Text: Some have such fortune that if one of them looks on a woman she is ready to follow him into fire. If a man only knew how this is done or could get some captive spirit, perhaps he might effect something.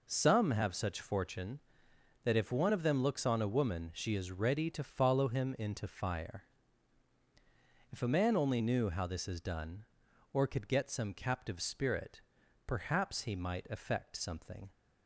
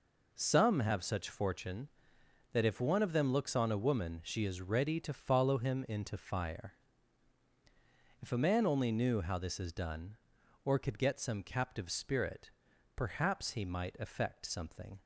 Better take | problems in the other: neither | none

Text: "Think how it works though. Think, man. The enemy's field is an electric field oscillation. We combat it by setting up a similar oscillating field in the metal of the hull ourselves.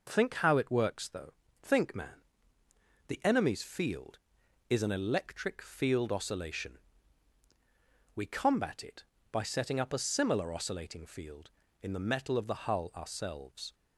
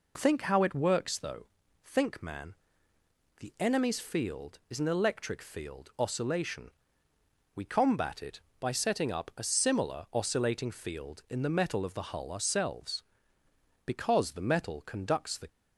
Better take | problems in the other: first | goes on to say "Because the metal conducts the"; from 13.8 s on; 1.6 s long

